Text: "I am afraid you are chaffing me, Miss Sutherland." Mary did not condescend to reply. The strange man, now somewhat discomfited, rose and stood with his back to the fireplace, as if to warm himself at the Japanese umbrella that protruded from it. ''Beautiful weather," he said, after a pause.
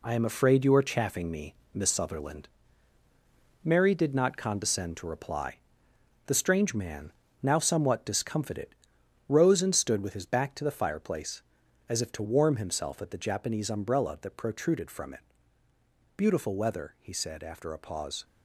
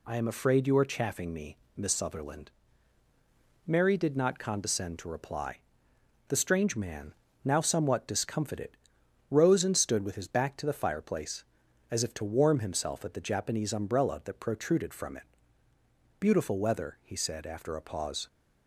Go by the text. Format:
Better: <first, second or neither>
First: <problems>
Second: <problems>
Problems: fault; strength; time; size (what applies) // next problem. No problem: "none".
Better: second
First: gets quieter; throughout; 6.5 dB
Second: none